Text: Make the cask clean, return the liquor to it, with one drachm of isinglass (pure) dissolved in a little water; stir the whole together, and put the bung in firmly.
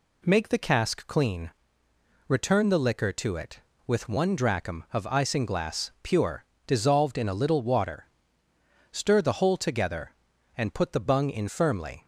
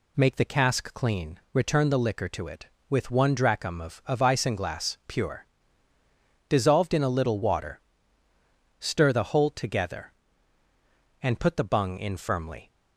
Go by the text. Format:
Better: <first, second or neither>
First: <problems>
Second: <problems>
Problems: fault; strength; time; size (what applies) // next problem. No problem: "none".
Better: first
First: none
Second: says "of" twice; at 4.0 s